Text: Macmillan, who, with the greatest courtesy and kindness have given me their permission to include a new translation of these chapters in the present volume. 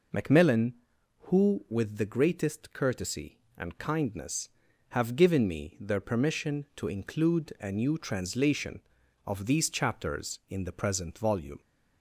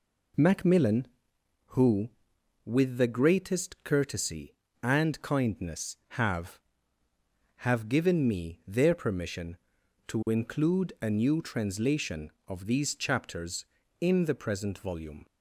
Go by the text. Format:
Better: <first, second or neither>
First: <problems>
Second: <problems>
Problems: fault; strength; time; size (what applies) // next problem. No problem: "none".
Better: first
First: none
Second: says "have" twice; at 7.5 s